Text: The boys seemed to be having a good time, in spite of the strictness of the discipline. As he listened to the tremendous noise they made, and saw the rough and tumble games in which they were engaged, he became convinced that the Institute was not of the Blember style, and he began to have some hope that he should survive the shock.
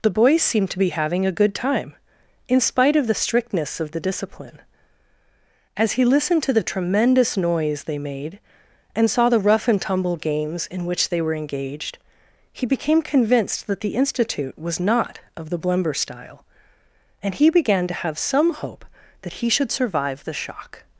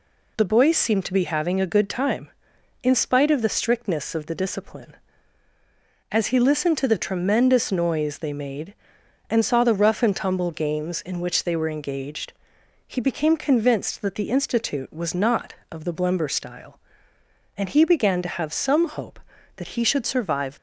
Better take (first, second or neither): first